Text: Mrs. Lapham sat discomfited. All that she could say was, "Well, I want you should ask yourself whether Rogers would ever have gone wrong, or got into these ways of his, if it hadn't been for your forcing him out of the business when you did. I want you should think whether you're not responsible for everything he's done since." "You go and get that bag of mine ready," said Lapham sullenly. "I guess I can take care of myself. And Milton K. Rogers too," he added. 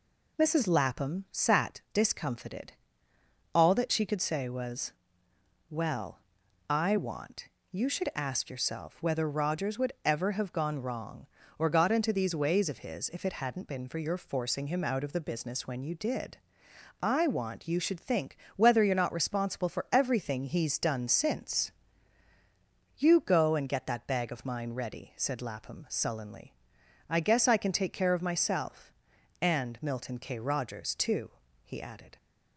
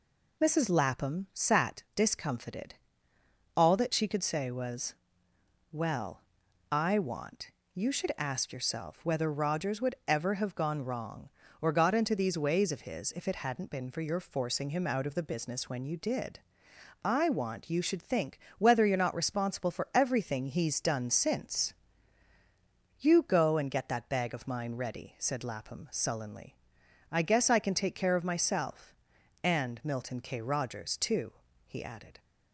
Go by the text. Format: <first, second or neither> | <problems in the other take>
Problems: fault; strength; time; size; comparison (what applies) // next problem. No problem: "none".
neither | pauses between "want" and "you"; slight; the same in both // pauses between "think" and "whether"; slight; the same in both